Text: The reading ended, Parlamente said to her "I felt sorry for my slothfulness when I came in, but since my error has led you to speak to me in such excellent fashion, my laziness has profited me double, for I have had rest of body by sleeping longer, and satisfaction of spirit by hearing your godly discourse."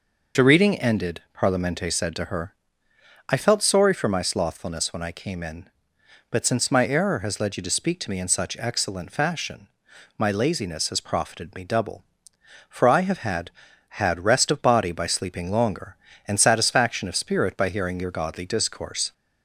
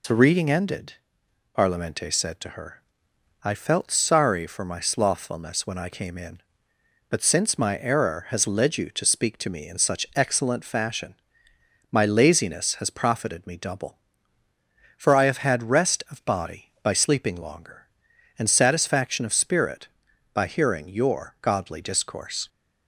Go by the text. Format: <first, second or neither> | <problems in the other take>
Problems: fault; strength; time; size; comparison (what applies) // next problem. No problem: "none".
second | pauses between "her" and "I"; noticeable; at 2.5 s; 0.78 s long; noticeable in the second // says "had" twice; at 13.8 s